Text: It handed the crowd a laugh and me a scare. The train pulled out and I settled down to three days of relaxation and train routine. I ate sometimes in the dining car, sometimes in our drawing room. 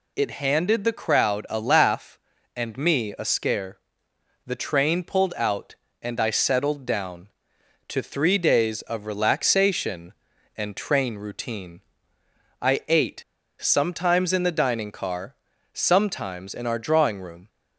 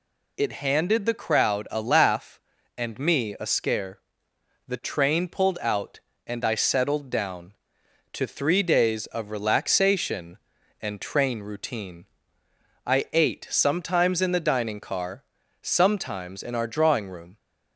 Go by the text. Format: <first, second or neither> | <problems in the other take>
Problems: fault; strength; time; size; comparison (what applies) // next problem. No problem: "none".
second | pauses between "ate" and "sometimes"; at 13.2 s; 0.40 s long